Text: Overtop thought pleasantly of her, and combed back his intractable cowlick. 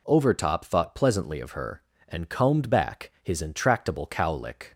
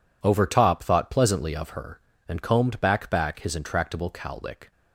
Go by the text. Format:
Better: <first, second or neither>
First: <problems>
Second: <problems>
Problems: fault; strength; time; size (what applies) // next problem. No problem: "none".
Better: first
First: none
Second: says "back" twice; at 3.1 s